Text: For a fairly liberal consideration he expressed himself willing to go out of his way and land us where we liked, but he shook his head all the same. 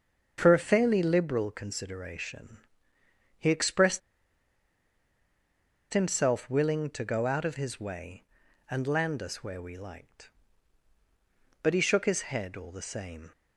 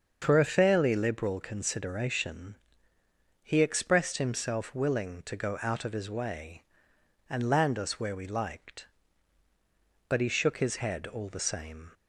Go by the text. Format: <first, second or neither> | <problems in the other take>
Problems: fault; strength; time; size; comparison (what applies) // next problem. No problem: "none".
second | starts louder than the rest; until 1.3 s; 6.5 dB; also in the second // pauses between "consideration" and "he"; noticeable; at 2.5 s; 0.78 s long; noticeable in the second // pauses between "expressed" and "himself"; strong; at 3.9 s; 1.9 s long